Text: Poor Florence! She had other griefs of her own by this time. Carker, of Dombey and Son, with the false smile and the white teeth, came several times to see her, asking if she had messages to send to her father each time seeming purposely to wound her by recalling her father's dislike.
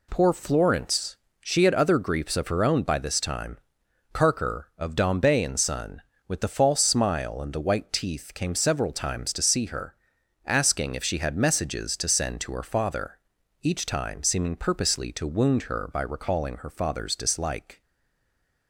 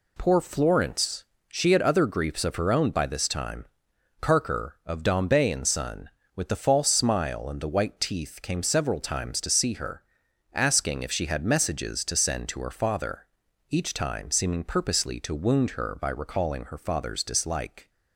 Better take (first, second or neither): second